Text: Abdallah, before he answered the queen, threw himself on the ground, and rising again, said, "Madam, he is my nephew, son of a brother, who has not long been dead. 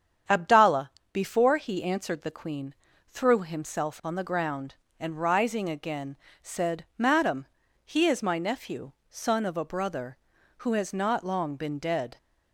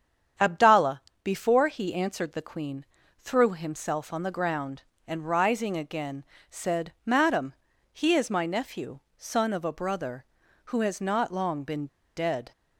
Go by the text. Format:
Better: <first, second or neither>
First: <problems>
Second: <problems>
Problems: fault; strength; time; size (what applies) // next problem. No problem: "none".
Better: first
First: starts louder than the rest; strong; until 1.5 s; 8 dB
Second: starts louder than the rest; strong; until 1.6 s; 8 dB // pauses between "been" and "dead"; slight; at 11.8 s; 0.29 s long